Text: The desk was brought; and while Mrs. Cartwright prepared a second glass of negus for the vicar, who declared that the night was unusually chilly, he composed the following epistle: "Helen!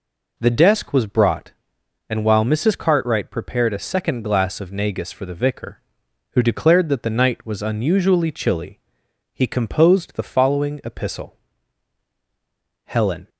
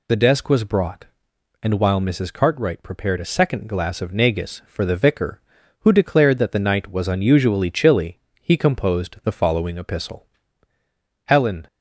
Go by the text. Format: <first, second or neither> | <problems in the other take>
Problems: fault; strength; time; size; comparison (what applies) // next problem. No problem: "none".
neither | none